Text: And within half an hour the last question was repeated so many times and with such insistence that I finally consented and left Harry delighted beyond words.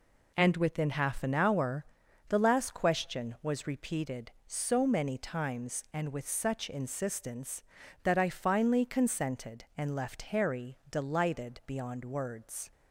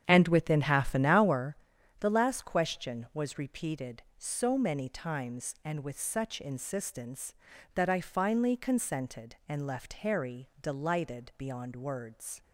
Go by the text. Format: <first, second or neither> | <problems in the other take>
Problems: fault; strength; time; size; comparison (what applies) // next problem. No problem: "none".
first | starts louder than the rest; strong; until 1.4 s; 8 dB // pauses between "hour" and "the"; at 1.5 s; 0.44 s long; also in the first